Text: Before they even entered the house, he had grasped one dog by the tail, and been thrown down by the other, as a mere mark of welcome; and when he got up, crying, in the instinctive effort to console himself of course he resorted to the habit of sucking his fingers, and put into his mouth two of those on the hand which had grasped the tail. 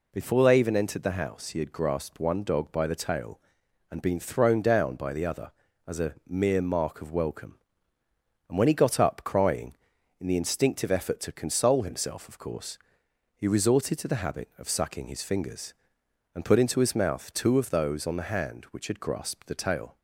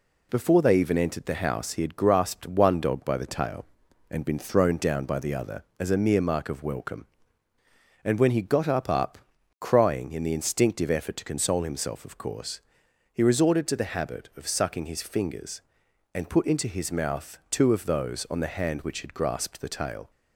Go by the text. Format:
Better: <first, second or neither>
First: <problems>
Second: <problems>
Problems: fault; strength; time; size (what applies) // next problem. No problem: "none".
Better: first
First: pauses between "course" and "he"; noticeable; at 12.7 s; 0.56 s long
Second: says "up" twice; at 8.8 s // pauses between "course" and "he"; noticeable; at 12.6 s; 0.52 s long